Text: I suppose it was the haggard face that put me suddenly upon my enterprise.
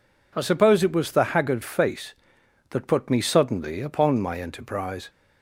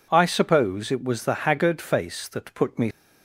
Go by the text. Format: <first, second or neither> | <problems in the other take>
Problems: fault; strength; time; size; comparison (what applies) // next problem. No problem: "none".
first | stops before "suddenly upon my enterprise"; at 2.9 s